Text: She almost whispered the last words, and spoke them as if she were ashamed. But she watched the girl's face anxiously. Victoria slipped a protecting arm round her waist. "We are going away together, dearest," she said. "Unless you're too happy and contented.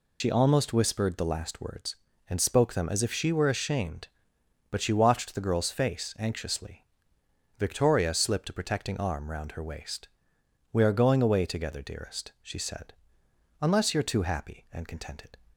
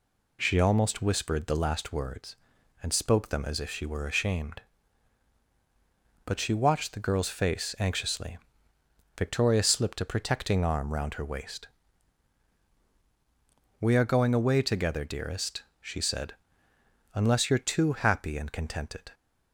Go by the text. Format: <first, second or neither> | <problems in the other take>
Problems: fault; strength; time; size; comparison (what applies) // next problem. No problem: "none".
second | loses the start of "She"; at 0.2 s; 80 ms